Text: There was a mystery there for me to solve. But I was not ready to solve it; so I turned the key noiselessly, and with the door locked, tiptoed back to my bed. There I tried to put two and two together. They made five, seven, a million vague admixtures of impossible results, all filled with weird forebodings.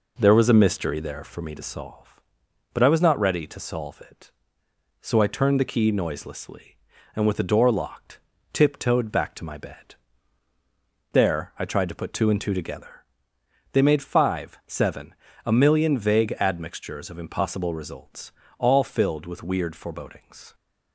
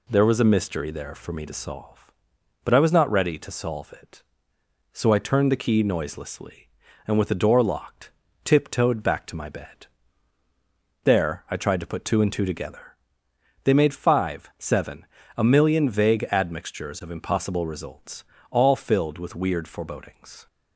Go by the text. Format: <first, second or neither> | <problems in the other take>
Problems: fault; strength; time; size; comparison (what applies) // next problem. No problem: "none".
second | starts louder than the rest; noticeable; until 1.4 s; 4 dB